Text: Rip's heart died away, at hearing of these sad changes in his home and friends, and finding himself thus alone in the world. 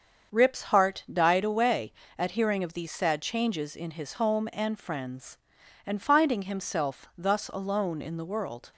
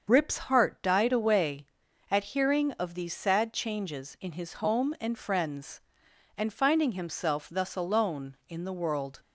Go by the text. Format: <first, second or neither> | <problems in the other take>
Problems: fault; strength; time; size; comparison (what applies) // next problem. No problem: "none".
neither | starts louder than the rest; the same in both